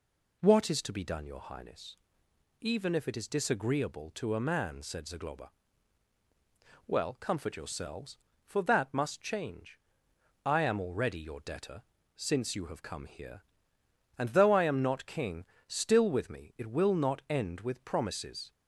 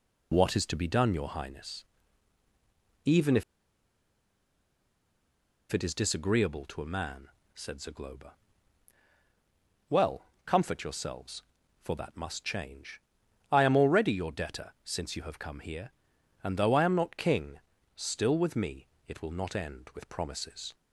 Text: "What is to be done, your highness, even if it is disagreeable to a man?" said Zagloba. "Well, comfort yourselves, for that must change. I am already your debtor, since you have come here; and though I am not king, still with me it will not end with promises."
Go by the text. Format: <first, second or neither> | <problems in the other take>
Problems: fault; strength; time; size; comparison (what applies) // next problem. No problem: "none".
first | pauses between "if" and "it"; strong; at 3.4 s; 2.3 s long // pauses between "me" and "it"; slight; at 18.8 s; 0.18 s long